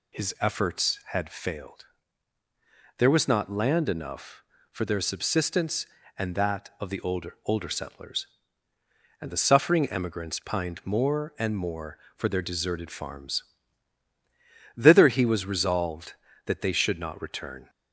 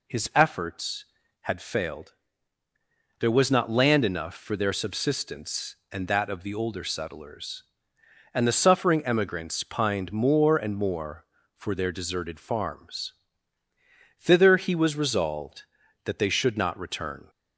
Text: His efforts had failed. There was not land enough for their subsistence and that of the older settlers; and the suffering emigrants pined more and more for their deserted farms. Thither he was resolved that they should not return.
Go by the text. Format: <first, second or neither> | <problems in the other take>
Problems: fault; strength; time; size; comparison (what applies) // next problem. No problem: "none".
second | says "older" twice; at 7.4 s